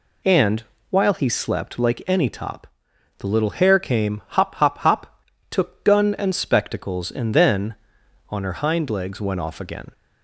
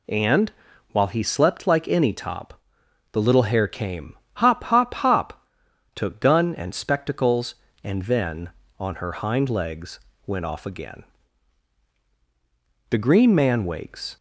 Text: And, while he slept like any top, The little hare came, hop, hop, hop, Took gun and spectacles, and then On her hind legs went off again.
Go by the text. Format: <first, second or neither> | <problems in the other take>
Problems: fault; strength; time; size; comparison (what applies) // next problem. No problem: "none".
first | pauses between "legs" and "went"; slight; at 9.9 s; 0.28 s long // goes on to say "The green man wakes"; noticeable; from 12.9 s on; 1.2 s long